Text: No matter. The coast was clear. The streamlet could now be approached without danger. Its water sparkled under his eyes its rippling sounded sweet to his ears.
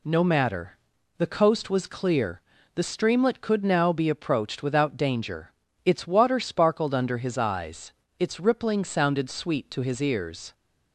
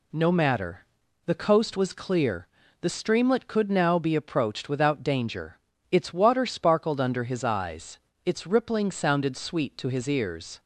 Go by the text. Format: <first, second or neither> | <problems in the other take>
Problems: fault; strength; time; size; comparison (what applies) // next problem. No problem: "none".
neither | pauses between "eyes" and "its"; slight; the same in both